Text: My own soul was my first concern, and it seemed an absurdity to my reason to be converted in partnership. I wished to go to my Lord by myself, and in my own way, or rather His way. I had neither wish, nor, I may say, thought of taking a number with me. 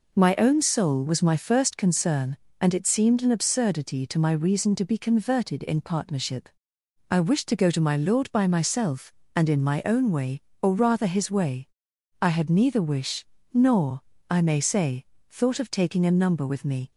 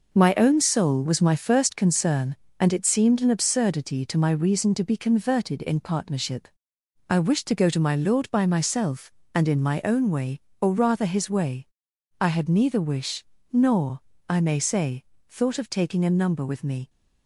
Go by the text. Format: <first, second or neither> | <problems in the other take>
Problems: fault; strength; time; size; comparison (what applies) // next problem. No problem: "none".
first | gets quieter; throughout; 7 dB